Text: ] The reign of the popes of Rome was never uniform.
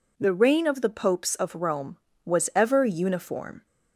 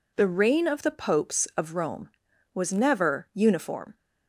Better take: second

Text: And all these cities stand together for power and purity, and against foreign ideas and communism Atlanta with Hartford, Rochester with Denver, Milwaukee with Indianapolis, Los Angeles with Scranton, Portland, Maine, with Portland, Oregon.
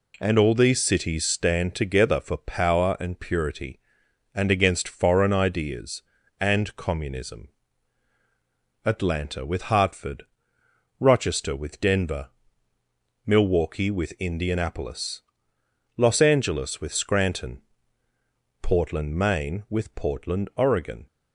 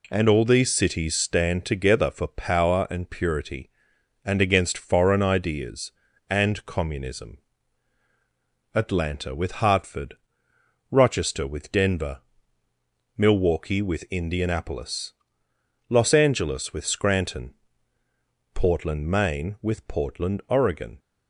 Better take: neither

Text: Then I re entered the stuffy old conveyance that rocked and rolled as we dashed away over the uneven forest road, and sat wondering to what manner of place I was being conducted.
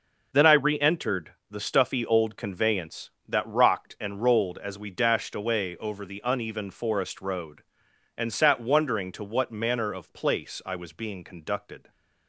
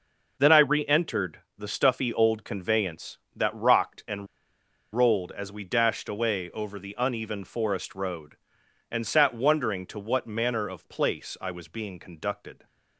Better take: first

